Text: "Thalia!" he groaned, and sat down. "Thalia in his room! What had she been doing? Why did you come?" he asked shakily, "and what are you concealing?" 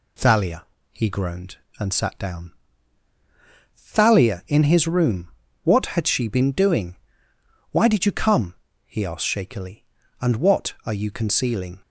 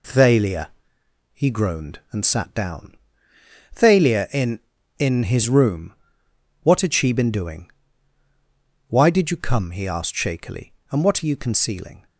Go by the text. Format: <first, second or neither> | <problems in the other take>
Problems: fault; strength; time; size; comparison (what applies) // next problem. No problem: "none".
first | says "in" twice; at 4.9 s